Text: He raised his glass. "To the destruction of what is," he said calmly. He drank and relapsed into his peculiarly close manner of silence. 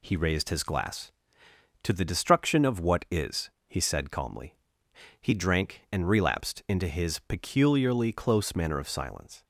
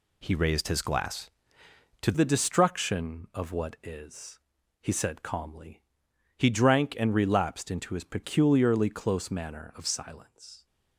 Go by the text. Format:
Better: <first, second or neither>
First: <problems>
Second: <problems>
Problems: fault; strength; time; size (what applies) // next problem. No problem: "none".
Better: first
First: none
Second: changes voice at "the"; from 2.1 s on; 8.5 s long